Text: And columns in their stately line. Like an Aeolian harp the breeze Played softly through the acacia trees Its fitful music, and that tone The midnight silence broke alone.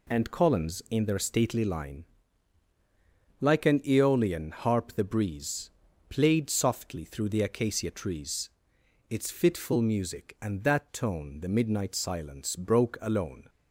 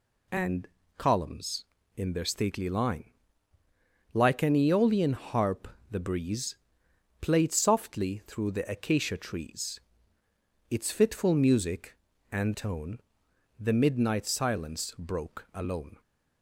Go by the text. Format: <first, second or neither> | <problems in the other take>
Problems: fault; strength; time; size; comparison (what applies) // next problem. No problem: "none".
first | pauses between "And" and "columns"; slight; at 0.6 s; 0.30 s long // pauses between "harp" and "the"; slight; at 5.6 s; 0.22 s long // pauses between "breeze" and "Played"; noticeable; at 6.5 s; 0.64 s long; also in the first // pauses between "trees" and "Its"; noticeable; at 9.8 s; 0.90 s long; noticeable in the first // skips "that"; at 12.5 s // pauses between "tone" and "The"; noticeable; at 12.9 s; 0.60 s long